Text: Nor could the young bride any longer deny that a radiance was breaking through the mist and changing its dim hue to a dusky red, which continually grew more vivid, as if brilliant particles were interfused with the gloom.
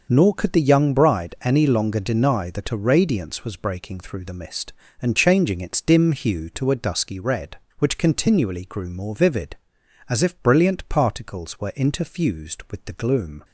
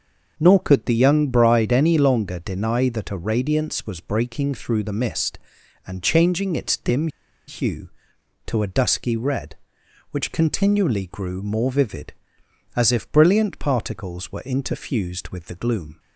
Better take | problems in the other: first | starts louder than the rest; until 1.3 s; 6 dB; also in the first // pauses between "dim" and "hue"; at 7.0 s; 0.39 s long

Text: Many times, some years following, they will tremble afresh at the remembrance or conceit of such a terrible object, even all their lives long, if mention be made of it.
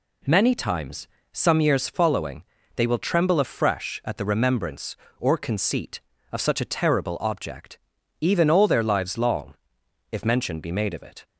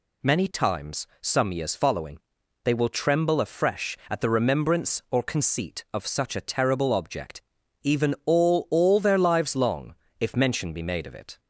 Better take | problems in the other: first | says "all" twice; at 8.6 s

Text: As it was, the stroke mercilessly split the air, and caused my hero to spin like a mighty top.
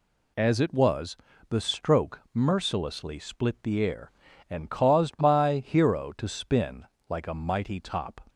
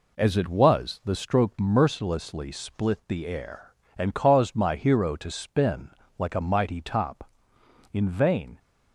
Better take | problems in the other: first | pauses between "spin" and "like"; slight; at 5.8 s; 0.30 s long; slight in the first // goes on to say "In vain"; noticeable; from 7.9 s on; 0.66 s long

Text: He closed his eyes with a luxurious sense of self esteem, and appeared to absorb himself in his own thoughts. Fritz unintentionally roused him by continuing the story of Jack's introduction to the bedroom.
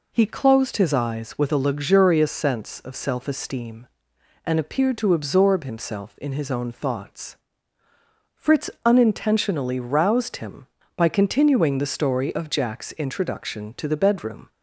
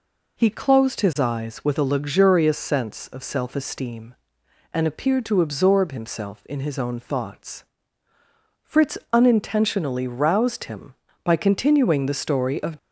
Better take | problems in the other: first | pauses between "Fritz" and "unintentionally"; slight; at 8.9 s; 0.16 s long; slight in the first // stops before "Jack's introduction to the bedroom"; at 12.7 s

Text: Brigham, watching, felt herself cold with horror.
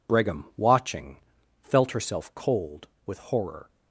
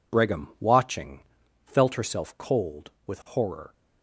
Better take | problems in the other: neither | none

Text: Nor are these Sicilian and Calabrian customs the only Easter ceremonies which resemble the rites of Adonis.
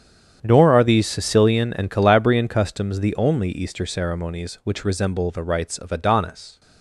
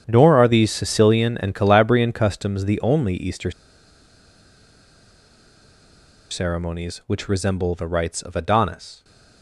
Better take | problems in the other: first | starts louder than the rest; strong; until 1.0 s; 8.5 dB; strong in the first // pauses between "Easter" and "ceremonies"; strong; at 3.5 s; 2.8 s long

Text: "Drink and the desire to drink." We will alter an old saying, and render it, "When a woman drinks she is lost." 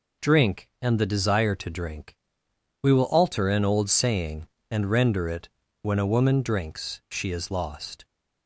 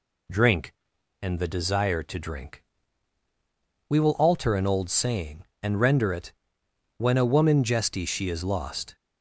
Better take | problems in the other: first | says "jesty" for "drinks"; at 7.6 s

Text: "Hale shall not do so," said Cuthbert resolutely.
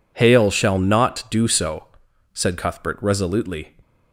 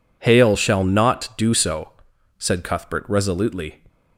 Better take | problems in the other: neither | none

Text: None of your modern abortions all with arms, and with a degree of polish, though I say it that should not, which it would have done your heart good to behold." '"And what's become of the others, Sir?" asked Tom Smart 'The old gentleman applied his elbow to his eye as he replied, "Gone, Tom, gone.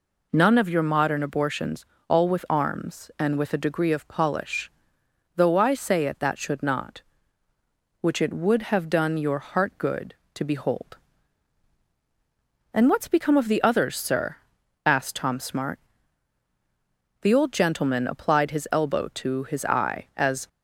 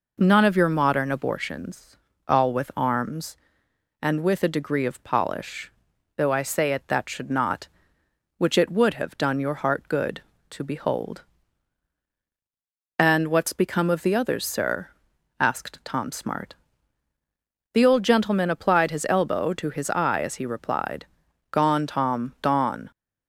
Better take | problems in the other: second | pauses between "abortions" and "all"; slight; at 1.8 s; 0.24 s long; slight in the second // pauses between "Smart" and "The"; strong; at 15.7 s; 1.4 s long; also in the second // stops before "he replied Gone Tom gone"; at 20.4 s

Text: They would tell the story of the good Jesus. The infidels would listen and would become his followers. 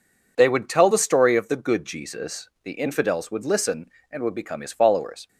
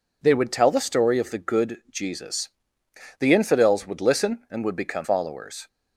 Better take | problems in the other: first | skips "his"; at 5.0 s

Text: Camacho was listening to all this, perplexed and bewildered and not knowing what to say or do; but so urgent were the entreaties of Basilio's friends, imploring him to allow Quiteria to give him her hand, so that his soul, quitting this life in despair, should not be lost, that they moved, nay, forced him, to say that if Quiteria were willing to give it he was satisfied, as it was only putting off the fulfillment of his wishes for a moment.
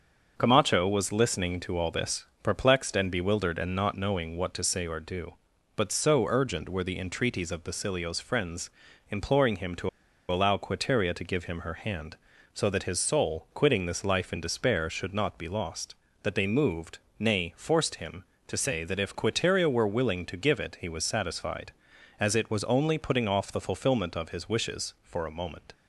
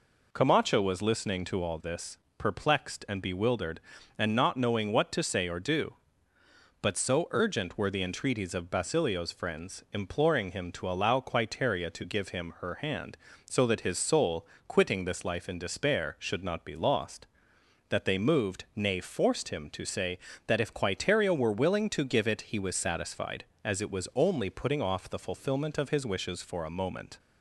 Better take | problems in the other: second | starts louder than the rest; until 1.3 s; 6.5 dB // pauses between "to" and "allow"; at 9.8 s; 0.41 s long

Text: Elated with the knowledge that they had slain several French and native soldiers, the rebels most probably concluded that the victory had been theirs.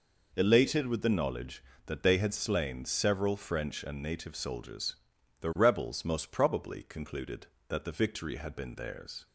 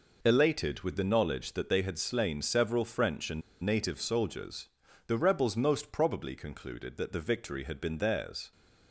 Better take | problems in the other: first | pauses between "and" and "native"; slight; at 3.4 s; 0.21 s long

